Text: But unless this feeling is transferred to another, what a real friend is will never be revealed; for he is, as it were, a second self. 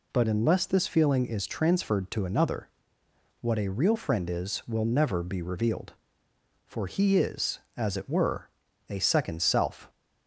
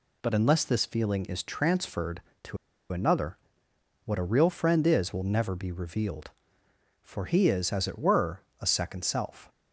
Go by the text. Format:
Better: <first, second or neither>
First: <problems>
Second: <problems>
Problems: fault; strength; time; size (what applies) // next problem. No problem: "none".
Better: first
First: none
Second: pauses between "to" and "another"; slight; at 2.5 s; 0.34 s long